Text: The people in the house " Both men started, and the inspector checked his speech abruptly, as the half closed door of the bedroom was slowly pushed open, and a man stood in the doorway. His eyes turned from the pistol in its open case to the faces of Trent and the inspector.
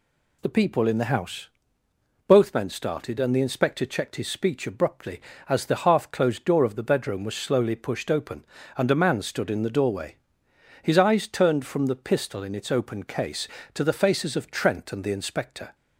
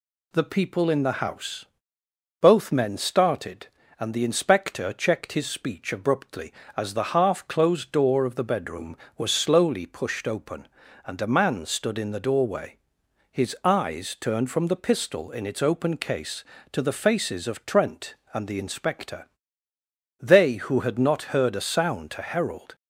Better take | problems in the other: first | goes on to say "They who had not heard a sound to herald"; strong; from 20.1 s on; 2.5 s long

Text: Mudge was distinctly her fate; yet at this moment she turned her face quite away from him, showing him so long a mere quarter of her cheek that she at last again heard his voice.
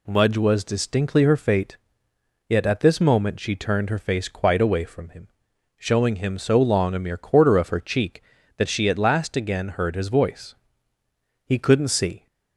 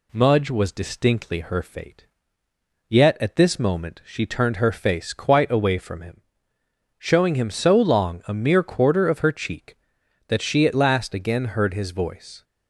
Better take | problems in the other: second | goes on to say "He couldn't see"; noticeable; from 11.4 s on; 0.82 s long

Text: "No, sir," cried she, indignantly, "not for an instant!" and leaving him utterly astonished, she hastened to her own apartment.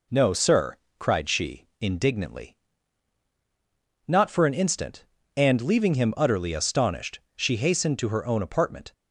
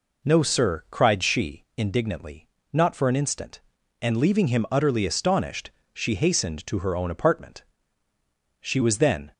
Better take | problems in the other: first | goes on to say "She was then"; noticeable; from 8.6 s on; 0.72 s long

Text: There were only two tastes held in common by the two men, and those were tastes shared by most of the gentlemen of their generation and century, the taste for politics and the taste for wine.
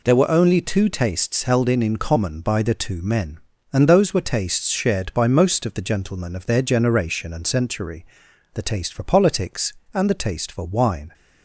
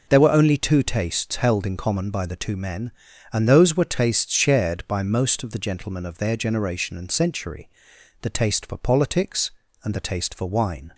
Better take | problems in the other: second | says "in" twice; at 1.8 s

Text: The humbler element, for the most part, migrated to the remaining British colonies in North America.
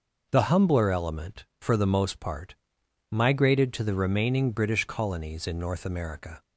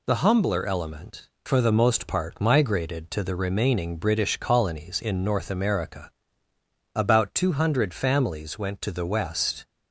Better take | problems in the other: first | goes on to say "About two hundred families went to the West"; strong; from 6.9 s on; 2.7 s long

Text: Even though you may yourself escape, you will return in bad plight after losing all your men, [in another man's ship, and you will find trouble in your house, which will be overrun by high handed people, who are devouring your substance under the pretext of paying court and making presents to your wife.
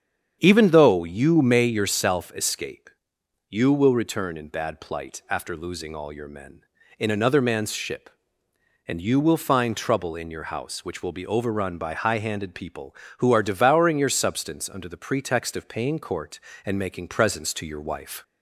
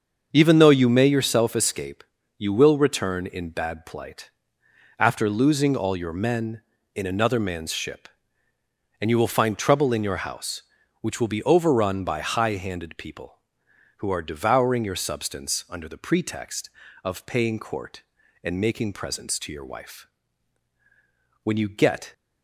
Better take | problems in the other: first | starts louder than the rest; until 1.3 s; 6.5 dB; strong in the first // pauses between "plight" and "after"; noticeable; at 4.3 s; 0.66 s long // goes on to say "When you get"; noticeable; from 21.4 s on; 0.70 s long

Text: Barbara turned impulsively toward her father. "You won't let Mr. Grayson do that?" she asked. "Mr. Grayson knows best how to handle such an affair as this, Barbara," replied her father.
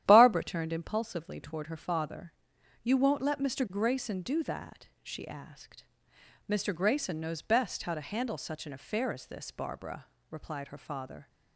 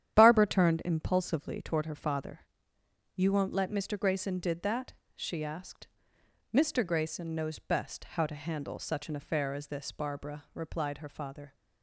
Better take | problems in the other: first | starts louder than the rest; strong; until 1.2 s; 10.5 dB; strong in the first // says "did" for "do"; at 4.3 s

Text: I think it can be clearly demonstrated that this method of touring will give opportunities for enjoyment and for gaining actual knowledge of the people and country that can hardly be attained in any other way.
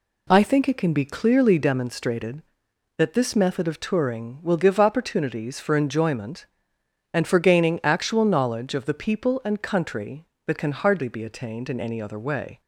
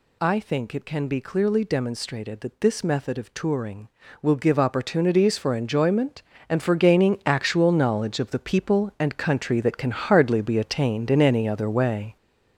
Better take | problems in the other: first | gets louder; noticeable; throughout; 6 dB

